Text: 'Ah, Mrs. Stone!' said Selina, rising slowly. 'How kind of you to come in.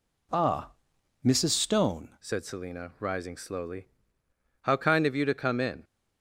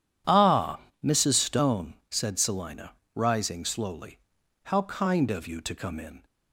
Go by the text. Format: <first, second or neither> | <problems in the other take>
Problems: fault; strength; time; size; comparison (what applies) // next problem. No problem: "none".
second | changes voice at "said"; from 2.1 s on; 3.7 s long